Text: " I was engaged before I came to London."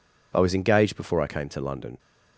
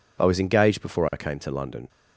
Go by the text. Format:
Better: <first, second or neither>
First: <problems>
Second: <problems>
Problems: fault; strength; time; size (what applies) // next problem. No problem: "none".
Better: neither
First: none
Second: none